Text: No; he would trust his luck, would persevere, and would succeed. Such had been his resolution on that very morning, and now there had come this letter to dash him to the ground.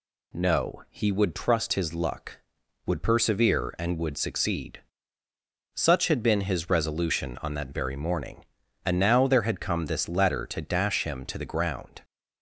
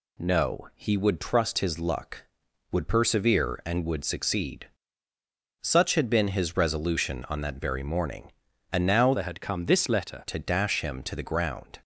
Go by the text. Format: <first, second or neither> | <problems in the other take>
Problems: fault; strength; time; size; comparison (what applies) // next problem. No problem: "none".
first | changes voice from "there" to "letter"; from 9.1 to 10.2 s; 1.1 s long